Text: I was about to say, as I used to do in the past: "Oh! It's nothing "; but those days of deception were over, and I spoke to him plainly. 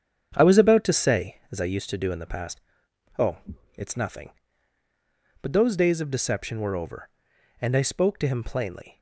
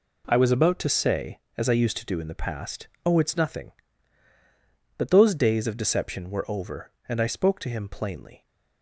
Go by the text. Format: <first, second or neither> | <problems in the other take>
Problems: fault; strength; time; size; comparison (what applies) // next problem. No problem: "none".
second | starts louder than the rest; strong; until 1.6 s; 8 dB